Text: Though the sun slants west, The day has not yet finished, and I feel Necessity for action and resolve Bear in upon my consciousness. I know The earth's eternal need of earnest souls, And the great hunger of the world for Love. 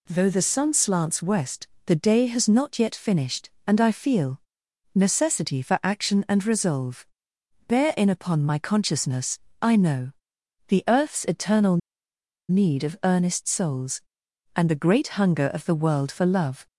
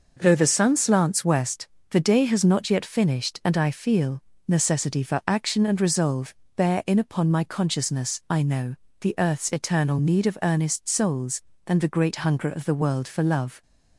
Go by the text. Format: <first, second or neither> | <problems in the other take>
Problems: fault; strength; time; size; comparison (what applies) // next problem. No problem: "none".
second | pauses between "feel" and "Necessity"; noticeable; at 4.3 s; 0.54 s long; slight in the second // pauses between "resolve" and "Bear"; noticeable; at 7.0 s; 0.62 s long; slight in the second // pauses between "know" and "The"; noticeable; at 10.1 s; 0.56 s long; slight in the second // pauses between "eternal" and "need"; noticeable; at 11.7 s; 0.71 s long